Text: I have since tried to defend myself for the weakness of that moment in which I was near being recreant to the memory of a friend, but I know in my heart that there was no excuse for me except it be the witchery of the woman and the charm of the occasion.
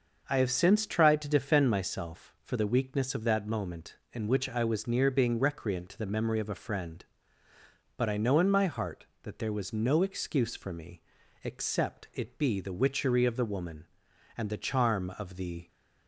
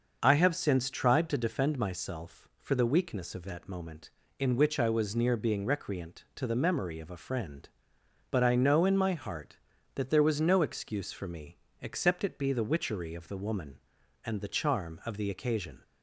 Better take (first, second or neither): second